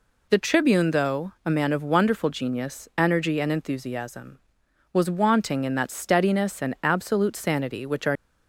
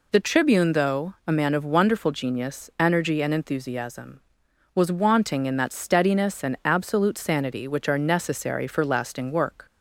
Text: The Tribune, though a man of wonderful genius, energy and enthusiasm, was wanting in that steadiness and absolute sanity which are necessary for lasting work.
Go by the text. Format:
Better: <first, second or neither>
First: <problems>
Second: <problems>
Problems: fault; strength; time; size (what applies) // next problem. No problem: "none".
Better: second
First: stops before "necessary for lasting work"; at 8.1 s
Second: none